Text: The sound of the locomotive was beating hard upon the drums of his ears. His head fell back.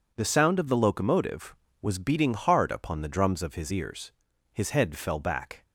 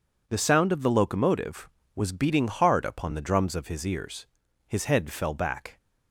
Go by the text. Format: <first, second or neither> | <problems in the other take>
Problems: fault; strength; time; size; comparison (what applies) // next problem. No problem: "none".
neither | none